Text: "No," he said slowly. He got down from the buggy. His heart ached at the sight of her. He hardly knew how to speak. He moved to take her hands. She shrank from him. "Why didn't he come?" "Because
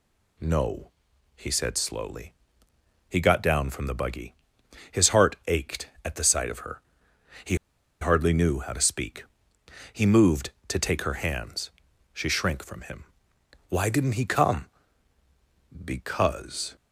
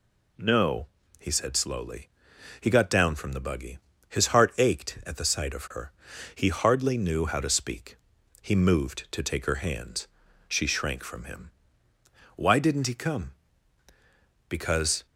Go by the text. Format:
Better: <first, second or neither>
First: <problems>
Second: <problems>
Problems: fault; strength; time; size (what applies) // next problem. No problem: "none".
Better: second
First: pauses between "He" and "hardly"; at 7.5 s; 0.45 s long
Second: none